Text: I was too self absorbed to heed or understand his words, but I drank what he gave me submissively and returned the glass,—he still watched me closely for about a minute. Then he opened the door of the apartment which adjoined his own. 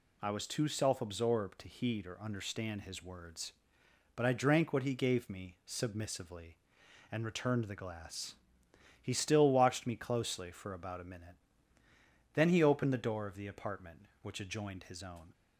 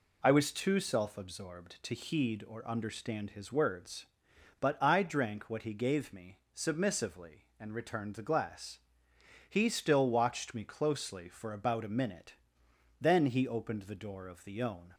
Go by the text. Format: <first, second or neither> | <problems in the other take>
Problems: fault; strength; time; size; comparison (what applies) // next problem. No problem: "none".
first | pauses between "me" and "submissively"; slight; at 6.3 s; 0.16 s long // skips "apartment which adjoined his"; at 14.6 s